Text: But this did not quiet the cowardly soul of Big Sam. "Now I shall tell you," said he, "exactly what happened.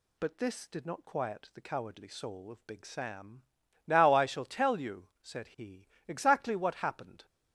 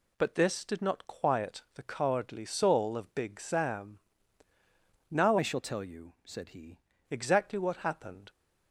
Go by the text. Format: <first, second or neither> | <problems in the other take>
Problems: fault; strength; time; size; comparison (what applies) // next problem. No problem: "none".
first | changes voice from "I" to "he"; from 5.3 to 6.7 s; 1.4 s long